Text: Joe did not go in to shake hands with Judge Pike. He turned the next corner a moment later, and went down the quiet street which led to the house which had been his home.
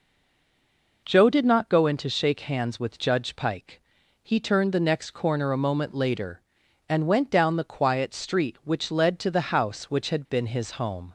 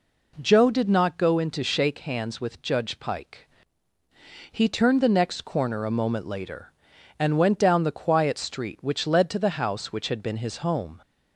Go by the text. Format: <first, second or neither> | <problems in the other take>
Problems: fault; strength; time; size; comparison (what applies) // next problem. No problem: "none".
second | stays silent before the first word; until 1.0 s; 1.0 s long